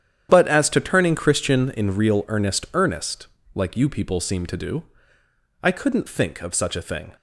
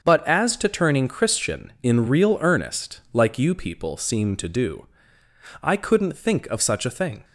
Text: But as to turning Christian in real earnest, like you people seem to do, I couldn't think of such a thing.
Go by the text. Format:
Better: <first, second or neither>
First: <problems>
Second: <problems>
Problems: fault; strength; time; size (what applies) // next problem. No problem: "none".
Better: second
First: starts louder than the rest; strong; until 1.3 s; 9.5 dB // says "earnest" twice; at 2.7 s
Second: starts louder than the rest; until 1.0 s; 7 dB